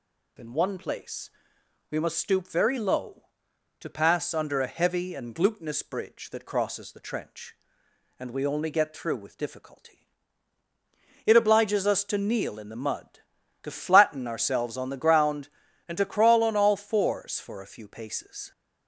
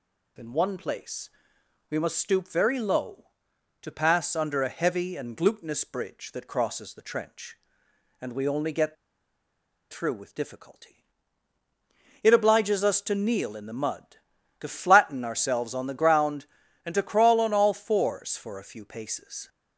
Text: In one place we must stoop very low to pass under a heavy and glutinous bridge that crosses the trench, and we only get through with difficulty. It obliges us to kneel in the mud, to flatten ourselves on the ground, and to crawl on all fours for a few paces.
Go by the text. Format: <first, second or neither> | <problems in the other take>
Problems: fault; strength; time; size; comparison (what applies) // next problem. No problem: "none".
first | pauses between "place" and "we"; noticeable; at 1.2 s; 0.60 s long; noticeable in the first // pauses between "get" and "through"; noticeable; at 8.9 s; 0.97 s long